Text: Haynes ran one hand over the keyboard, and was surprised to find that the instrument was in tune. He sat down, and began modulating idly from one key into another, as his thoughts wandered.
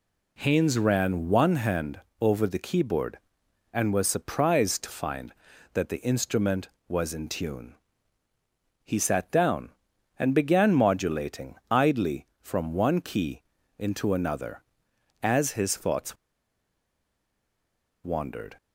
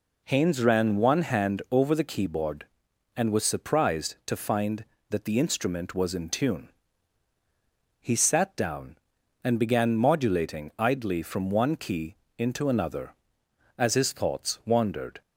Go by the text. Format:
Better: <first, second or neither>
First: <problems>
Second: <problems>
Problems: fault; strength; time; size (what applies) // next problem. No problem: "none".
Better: second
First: pauses between "hand" and "over"; slight; at 2.0 s; 0.20 s long // pauses between "modulating" and "idly"; slight; at 11.5 s; 0.16 s long // pauses between "key" and "into"; at 13.4 s; 0.38 s long // pauses between "thoughts" and "wandered"; strong; at 16.1 s; 1.8 s long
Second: pauses between "key" and "into"; slight; at 12.1 s; 0.22 s long